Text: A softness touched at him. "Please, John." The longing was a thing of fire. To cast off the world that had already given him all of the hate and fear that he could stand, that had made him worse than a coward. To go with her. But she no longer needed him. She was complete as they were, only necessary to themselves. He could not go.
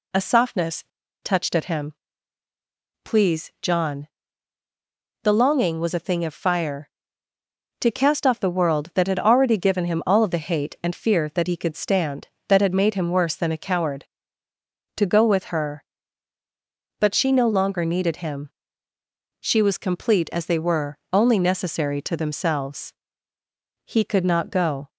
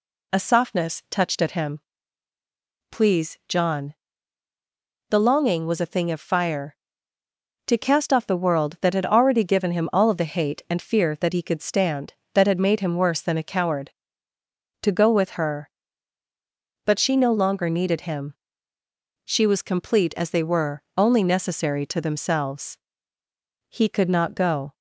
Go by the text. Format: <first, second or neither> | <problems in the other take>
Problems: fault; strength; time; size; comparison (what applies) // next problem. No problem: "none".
second | pauses between "softness" and "touched"; at 0.8 s; 0.38 s long